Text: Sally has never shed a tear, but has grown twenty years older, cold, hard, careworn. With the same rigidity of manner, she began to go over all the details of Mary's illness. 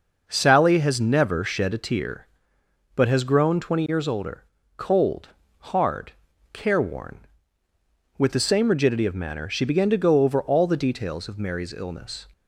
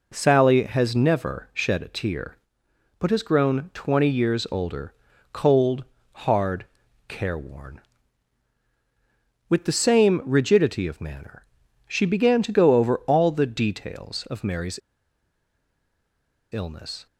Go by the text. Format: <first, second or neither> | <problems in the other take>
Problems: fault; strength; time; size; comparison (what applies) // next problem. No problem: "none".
first | pauses between "Mary's" and "illness"; strong; at 14.7 s; 1.7 s long